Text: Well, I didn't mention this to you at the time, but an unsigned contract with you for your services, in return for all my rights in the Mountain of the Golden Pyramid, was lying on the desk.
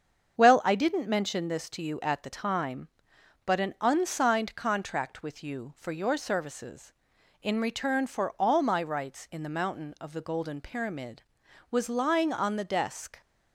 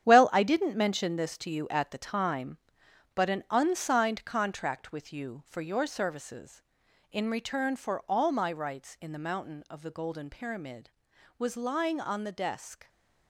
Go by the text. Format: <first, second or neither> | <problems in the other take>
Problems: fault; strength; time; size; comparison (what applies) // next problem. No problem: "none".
first | gets quieter; strong; throughout; 9 dB // starts louder than the rest; strong; until 1.1 s; 9.5 dB; strong in the first